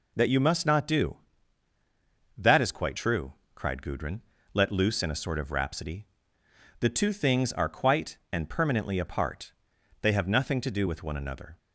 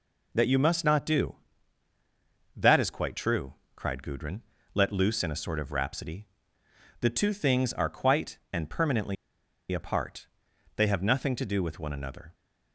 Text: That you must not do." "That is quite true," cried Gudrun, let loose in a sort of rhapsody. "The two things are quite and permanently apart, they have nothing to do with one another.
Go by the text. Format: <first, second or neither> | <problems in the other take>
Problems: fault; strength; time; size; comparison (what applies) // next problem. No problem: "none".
first | pauses between "permanently" and "apart"; noticeable; at 9.1 s; 0.56 s long